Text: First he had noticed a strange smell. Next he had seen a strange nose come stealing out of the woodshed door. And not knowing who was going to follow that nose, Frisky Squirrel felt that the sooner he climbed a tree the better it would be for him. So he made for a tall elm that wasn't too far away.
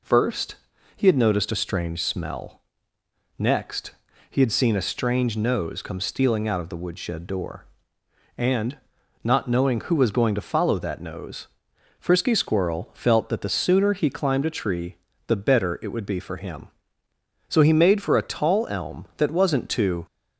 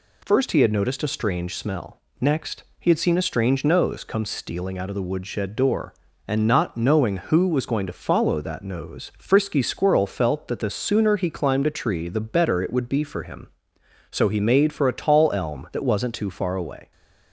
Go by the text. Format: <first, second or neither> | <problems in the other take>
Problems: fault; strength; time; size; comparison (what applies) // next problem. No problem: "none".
second | pauses between "First" and "he"; at 0.5 s; 0.40 s long // pauses between "Next" and "he"; at 3.9 s; 0.38 s long; slight in the second // pauses between "And" and "not"; noticeable; at 8.7 s; 0.46 s long // pauses between "tree" and "the"; slight; at 14.9 s; 0.32 s long // stops before "far away"; at 20.0 s